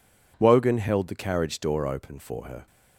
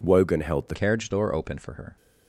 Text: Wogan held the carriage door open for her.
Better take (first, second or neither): first